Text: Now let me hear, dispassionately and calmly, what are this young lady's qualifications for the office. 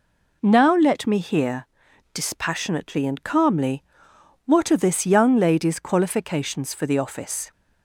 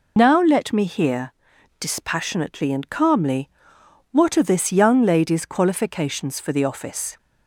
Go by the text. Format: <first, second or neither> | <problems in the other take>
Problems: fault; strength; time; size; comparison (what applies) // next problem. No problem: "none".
first | loses the start of "Now"; at 0.1 s; 90 ms